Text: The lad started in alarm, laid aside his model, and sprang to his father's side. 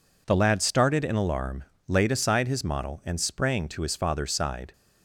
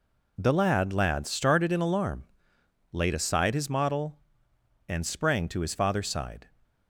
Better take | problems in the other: first | says "lad" twice; at 0.9 s

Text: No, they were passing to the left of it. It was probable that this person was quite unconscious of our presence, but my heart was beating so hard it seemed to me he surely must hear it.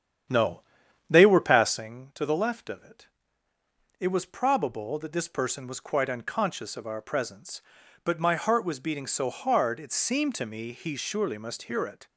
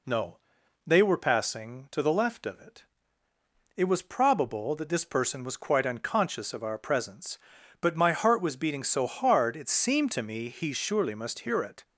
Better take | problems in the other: second | starts louder than the rest; strong; until 2.0 s; 9 dB

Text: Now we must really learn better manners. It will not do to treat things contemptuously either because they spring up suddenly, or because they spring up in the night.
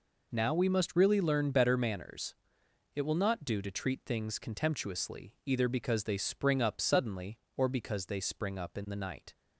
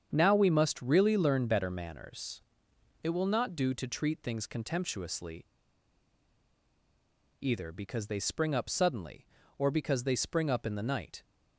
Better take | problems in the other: first | starts louder than the rest; strong; until 1.1 s; 7.5 dB // pauses between "contemptuously" and "either"; strong; at 5.4 s; 1.9 s long

